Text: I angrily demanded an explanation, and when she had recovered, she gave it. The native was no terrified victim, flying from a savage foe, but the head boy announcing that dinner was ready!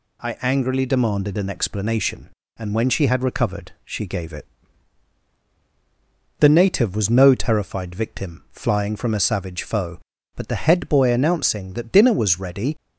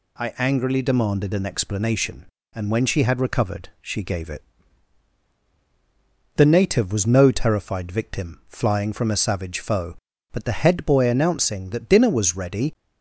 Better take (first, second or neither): neither